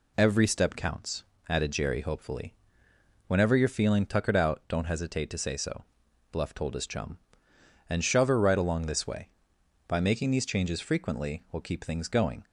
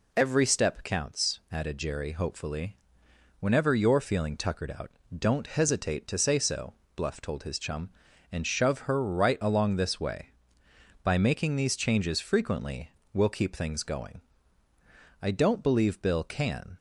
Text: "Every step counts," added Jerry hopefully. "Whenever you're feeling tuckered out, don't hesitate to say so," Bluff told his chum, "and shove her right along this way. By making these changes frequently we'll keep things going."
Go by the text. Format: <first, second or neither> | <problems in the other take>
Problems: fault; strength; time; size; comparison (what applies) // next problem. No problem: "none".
first | pauses between "frequently" and "we'll"; slight; at 12.8 s; 0.24 s long // goes on to say "I don't believe Bill can"; from 15.2 s on; 1.5 s long